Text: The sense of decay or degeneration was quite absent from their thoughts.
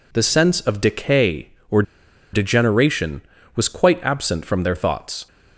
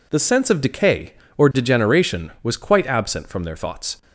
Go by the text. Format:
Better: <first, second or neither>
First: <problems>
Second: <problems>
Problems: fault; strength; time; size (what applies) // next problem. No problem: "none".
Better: second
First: pauses between "or" and "degeneration"; noticeable; at 1.8 s; 0.50 s long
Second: none